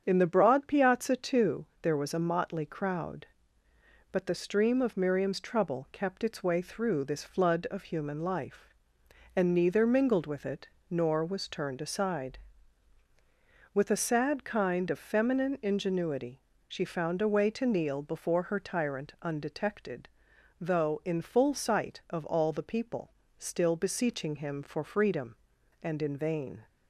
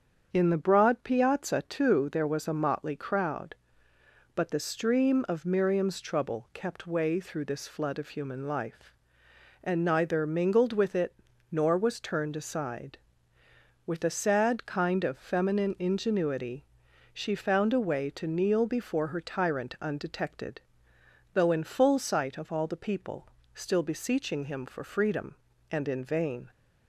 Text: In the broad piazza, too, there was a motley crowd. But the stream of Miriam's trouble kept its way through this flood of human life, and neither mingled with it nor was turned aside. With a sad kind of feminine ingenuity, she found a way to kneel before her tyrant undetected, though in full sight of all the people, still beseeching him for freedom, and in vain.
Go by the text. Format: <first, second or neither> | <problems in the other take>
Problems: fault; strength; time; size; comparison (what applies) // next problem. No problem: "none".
first | starts louder than the rest; strong; until 1.3 s; 7.5 dB; strong in the first // skips "its"; at 6.8 s // pauses between "it" and "nor"; at 11.1 s; 0.38 s long; slight in the first